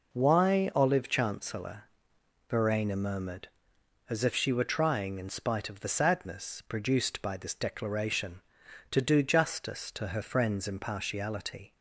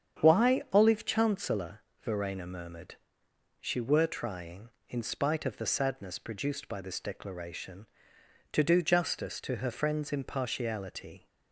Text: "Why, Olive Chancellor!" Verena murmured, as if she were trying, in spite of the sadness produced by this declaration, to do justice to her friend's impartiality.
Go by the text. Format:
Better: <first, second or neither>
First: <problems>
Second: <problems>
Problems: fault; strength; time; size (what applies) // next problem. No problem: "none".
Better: first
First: none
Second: starts louder than the rest; strong; until 1.2 s; 8 dB // skips "as if"; at 3.2 s